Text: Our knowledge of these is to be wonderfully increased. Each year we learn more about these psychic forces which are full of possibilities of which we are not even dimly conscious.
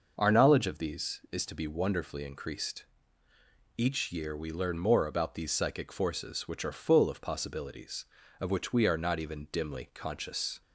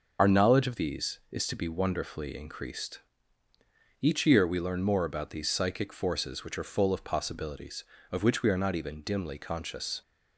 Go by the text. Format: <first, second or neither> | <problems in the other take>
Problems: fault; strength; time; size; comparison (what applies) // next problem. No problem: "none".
first | loses the start of "Our"; at 0.1 s; 40 ms